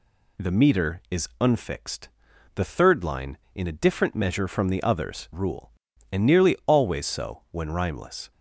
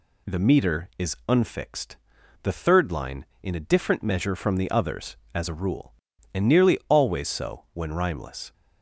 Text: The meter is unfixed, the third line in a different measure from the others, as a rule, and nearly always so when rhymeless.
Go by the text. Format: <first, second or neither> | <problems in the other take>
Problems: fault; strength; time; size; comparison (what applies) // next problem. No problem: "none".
second | skips "as a"; at 5.3 s